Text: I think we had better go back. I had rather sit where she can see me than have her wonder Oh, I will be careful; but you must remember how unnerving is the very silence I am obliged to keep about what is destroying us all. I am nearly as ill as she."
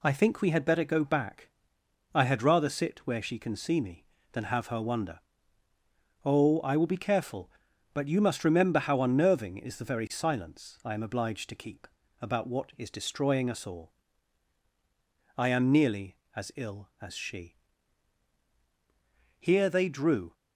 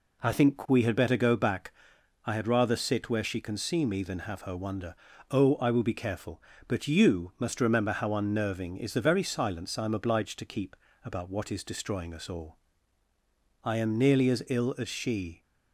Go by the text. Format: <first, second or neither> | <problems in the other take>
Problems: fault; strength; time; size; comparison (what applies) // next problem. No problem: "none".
second | pauses between "wonder" and "Oh"; at 5.1 s; 1.0 s long; also in the second // pauses between "keep" and "about"; slight; at 11.8 s; 0.32 s long; slight in the second // goes on to say "Here they drew"; noticeable; from 19.3 s on; 0.94 s long